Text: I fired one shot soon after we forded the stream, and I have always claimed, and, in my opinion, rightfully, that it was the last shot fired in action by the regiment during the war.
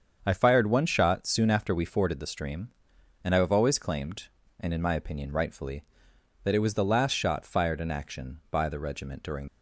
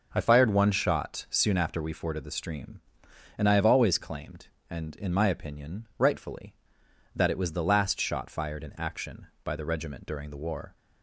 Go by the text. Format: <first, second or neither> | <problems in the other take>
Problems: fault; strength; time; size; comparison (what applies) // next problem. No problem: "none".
second | starts louder than the rest; strong; until 1.2 s; 7 dB // stops before "the war"; at 9.4 s